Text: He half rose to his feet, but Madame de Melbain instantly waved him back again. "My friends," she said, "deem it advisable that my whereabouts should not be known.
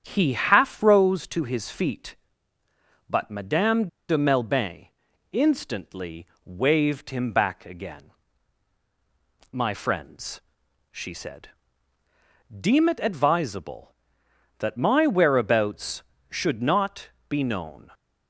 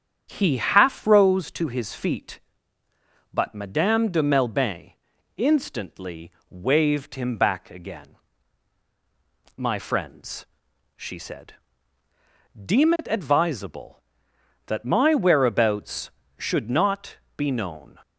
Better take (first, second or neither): second